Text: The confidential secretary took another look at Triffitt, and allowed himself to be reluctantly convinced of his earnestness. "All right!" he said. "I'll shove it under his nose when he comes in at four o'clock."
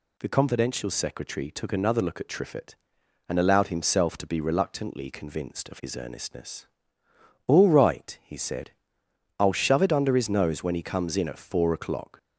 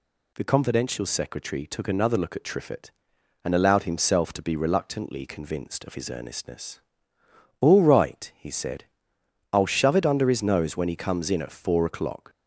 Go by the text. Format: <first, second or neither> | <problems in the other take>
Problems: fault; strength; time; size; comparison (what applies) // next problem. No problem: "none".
neither | none